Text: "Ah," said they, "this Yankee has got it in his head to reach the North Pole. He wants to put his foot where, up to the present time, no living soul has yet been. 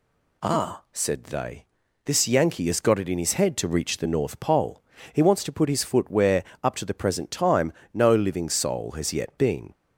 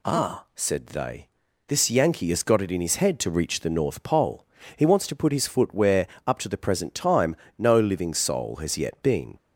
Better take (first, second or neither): neither